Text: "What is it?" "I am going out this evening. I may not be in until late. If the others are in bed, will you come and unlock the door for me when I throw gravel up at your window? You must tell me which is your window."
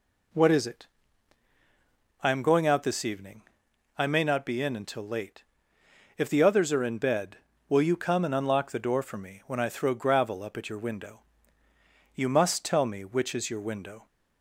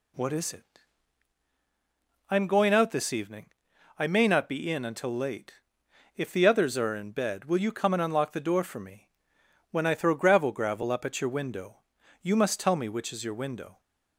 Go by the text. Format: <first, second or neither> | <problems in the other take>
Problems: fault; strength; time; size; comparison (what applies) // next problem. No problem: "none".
first | pauses between "me" and "when"; noticeable; at 9.0 s; 0.62 s long // says "gravel" twice; at 10.5 s